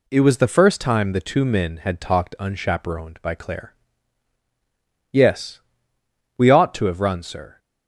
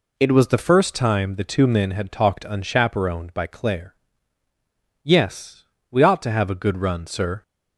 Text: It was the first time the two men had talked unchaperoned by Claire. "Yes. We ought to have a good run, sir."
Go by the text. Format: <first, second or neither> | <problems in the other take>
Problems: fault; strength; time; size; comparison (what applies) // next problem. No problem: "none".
second | skips "a good"; at 7.0 s